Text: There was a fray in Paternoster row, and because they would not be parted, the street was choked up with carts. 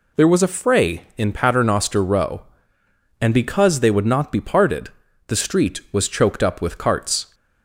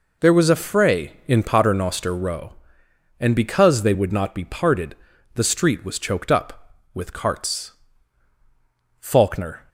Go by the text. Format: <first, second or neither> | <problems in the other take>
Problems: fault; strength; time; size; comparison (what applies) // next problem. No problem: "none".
first | goes on to say "FAULKNER"; noticeable; from 8.9 s on; 0.68 s long